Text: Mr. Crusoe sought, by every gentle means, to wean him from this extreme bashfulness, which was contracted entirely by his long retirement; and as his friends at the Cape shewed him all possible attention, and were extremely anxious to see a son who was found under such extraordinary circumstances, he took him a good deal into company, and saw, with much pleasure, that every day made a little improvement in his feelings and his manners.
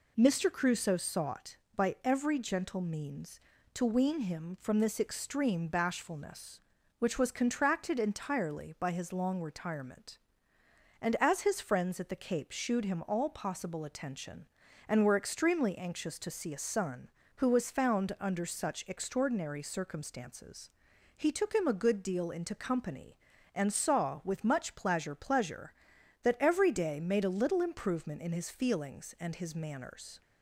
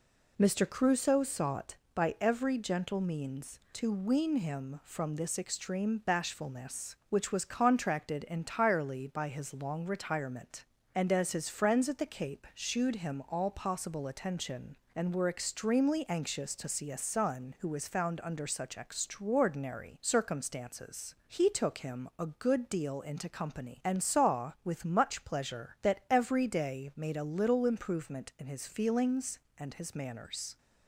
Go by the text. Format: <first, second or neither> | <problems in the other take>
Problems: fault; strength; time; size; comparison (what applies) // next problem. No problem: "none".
second | says "pleasure" twice; at 25.1 s